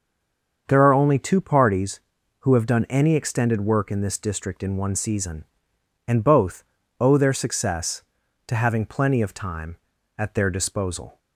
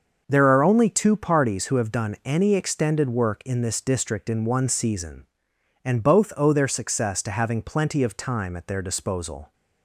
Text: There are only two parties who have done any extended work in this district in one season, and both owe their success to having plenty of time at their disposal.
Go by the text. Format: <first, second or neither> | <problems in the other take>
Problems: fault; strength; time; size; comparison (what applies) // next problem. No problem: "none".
second | stays silent before the first word; slight; until 0.6 s; 0.6 s long // starts louder than the rest; until 1.6 s; 6.5 dB; also in the second // pauses between "both" and "owe"; slight; at 6.6 s; 0.36 s long